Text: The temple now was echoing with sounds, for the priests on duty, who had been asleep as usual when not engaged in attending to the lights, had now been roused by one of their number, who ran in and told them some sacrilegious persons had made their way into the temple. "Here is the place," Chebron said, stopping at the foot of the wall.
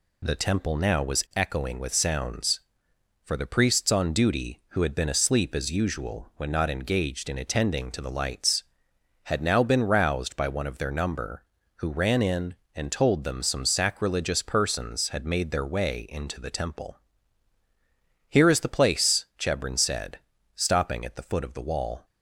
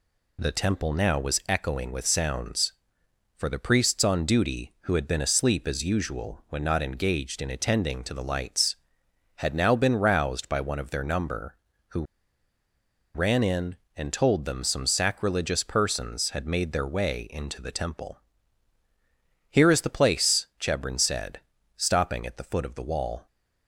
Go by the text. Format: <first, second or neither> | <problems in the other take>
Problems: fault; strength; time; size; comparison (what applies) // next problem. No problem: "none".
first | pauses between "who" and "ran"; at 12.0 s; 1.0 s long